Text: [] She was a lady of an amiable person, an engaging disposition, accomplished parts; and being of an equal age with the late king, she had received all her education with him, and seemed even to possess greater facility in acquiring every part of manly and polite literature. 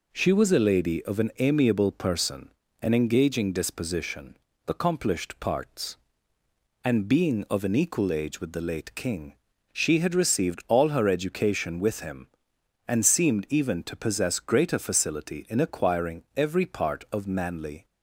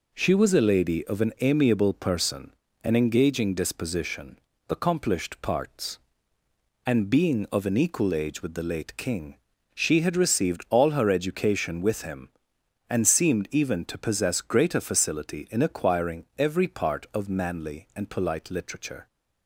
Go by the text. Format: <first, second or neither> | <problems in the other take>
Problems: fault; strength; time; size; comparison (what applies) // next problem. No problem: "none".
second | stops before "and polite literature"; at 17.8 s